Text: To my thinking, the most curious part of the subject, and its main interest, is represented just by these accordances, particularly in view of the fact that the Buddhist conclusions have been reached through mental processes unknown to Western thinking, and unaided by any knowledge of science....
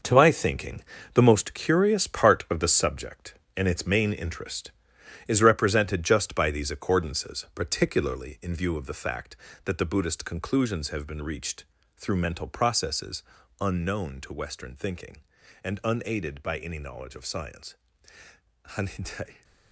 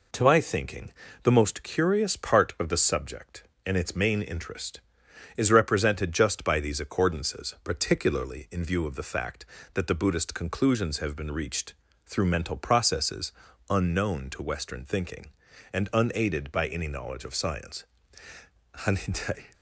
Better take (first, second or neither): second